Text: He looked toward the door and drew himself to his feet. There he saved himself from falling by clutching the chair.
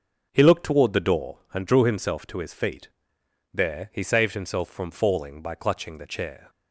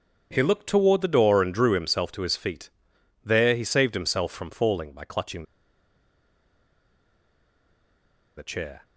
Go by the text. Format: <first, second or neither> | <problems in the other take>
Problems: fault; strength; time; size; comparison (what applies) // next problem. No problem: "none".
first | starts louder than the rest; strong; until 1.3 s; 7.5 dB; also in the first // pauses between "clutching" and "the"; strong; at 5.4 s; 2.9 s long